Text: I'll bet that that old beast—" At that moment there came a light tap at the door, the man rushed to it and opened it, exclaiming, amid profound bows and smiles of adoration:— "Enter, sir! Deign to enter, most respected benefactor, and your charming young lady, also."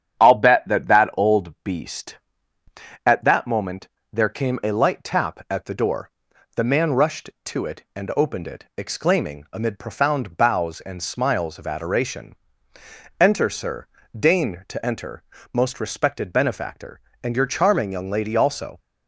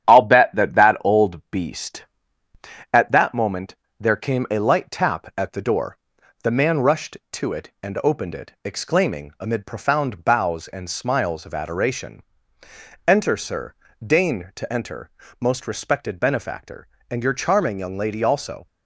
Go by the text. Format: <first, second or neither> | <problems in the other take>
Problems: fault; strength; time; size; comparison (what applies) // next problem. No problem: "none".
first | gets quieter; throughout; 4 dB // starts louder than the rest; strong; until 1.0 s; 10.5 dB; strong in the first // pauses between "moment" and "there"; slight; at 3.7 s; 0.24 s long; slight in the first